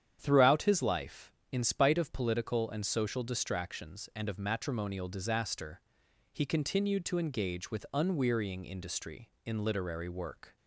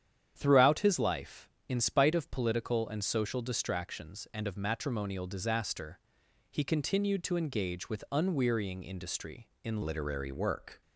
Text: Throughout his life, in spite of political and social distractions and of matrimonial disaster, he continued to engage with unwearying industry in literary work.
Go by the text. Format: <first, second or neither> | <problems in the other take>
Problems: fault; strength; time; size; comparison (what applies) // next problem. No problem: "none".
first | starts louder than the rest; strong; until 1.3 s; 9 dB; strong in the first // changes voice at "literary"; from 9.8 s on; 1.0 s long